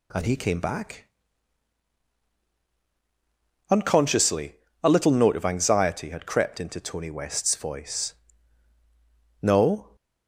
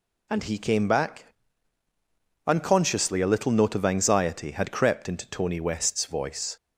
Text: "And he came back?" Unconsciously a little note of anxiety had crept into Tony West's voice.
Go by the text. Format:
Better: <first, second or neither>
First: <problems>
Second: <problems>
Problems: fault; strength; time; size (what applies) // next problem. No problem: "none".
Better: second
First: pauses between "Unconsciously" and "a"; slight; at 4.5 s; 0.26 s long // goes on to say "No"; from 9.4 s on; 0.54 s long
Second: none